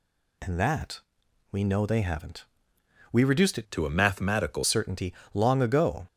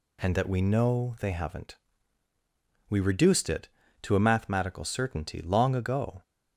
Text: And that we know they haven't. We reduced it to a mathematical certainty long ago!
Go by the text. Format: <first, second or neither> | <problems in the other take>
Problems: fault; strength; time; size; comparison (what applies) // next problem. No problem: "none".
second | pauses between "that" and "we"; noticeable; at 1.0 s; 0.50 s long // changes voice from "to" to "mathematical"; from 3.7 to 4.6 s; 0.9 s long // pauses between "certainty" and "long"; slight; at 5.1 s; 0.20 s long